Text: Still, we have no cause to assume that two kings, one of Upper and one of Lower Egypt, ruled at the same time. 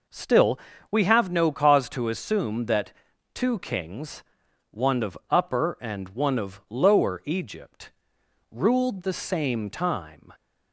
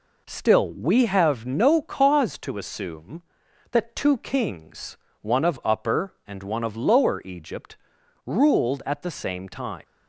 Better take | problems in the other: second | pauses between "that" and "two"; at 2.9 s; 0.42 s long // skips "at"; at 9.0 s

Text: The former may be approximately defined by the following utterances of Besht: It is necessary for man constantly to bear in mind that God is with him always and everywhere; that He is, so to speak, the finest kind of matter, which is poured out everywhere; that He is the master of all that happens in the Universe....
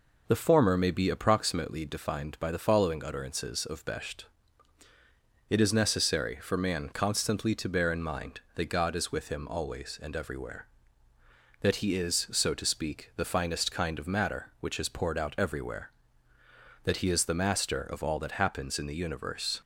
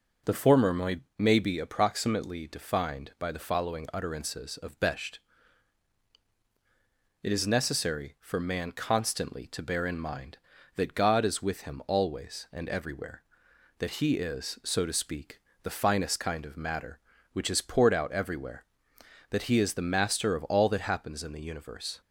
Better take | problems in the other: first | says "may" twice; at 1.1 s

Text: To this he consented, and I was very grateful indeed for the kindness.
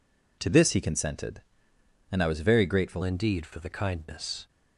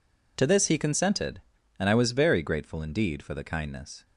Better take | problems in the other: second | changes voice at "indeed"; from 3.0 s on; 1.4 s long

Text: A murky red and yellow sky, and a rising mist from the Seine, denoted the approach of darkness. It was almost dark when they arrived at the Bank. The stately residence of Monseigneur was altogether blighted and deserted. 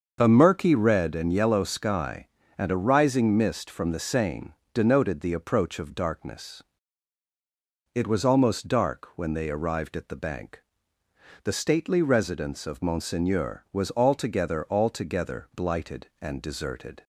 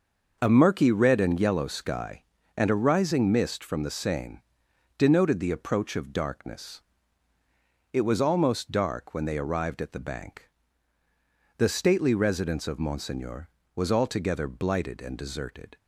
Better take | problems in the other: second | starts louder than the rest; until 1.2 s; 6.5 dB; noticeable in the second // says "altogether" twice; at 14.6 s

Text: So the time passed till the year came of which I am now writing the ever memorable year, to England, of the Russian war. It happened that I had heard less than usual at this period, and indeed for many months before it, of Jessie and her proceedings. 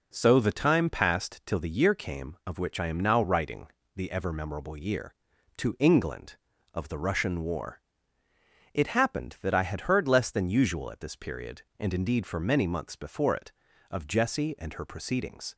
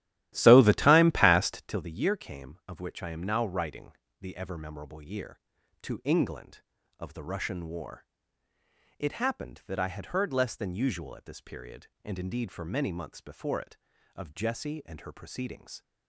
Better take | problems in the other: first | starts louder than the rest; strong; until 1.8 s; 14 dB // pauses between "writing" and "the"; slight; at 3.9 s; 0.28 s long; slight in the first

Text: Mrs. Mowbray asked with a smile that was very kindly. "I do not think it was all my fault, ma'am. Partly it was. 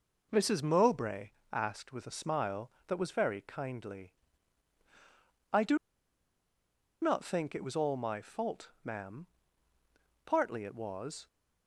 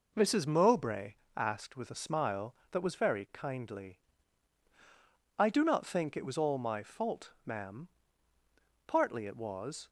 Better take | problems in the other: second | pauses between "Mowbray" and "asked"; slight; at 1.3 s; 0.20 s long; slight in the second // pauses between "do" and "not"; strong; at 5.7 s; 1.2 s long

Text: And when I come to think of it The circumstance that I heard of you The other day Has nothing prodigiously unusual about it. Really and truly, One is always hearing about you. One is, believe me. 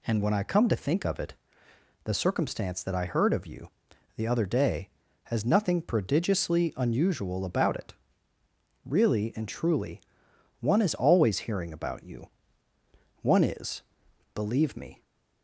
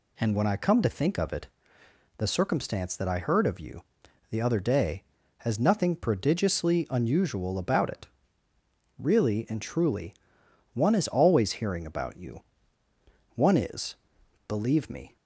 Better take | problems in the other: neither | pauses between "it" and "The"; noticeable; the same in both // pauses between "you" and "The"; noticeable; the same in both

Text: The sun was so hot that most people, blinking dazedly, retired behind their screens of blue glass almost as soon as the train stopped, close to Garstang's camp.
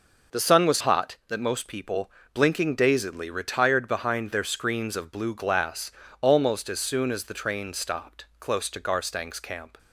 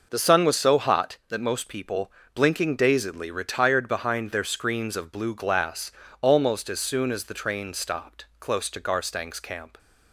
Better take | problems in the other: second | skips "so"; at 0.7 s // pauses between "glass" and "almost"; slight; at 5.9 s; 0.30 s long; slight in the second

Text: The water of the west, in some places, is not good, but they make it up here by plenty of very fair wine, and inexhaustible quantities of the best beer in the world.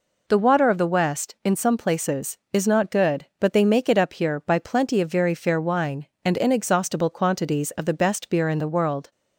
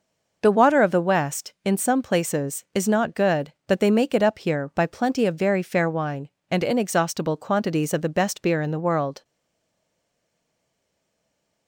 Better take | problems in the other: first | stays silent after the last word; from 9.2 s on; 2.4 s long

